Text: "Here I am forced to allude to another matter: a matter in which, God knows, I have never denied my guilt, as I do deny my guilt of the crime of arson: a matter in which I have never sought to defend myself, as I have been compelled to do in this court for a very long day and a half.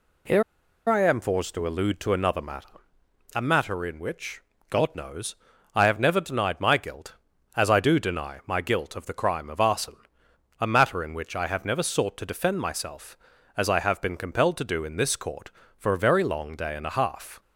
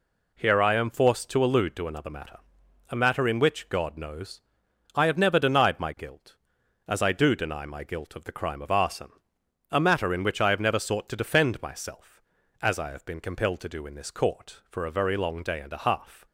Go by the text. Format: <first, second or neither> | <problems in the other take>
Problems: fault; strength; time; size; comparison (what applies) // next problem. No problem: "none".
second | pauses between "Here" and "I"; at 0.4 s; 0.45 s long